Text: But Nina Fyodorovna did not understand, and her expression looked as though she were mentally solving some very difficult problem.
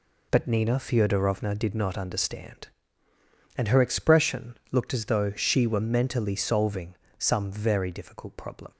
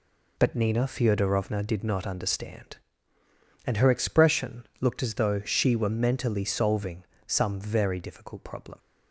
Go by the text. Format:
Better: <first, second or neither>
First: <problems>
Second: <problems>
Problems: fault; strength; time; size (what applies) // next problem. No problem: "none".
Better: neither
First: pauses between "solving" and "some"; slight; at 6.9 s; 0.22 s long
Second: pauses between "solving" and "some"; slight; at 7.0 s; 0.21 s long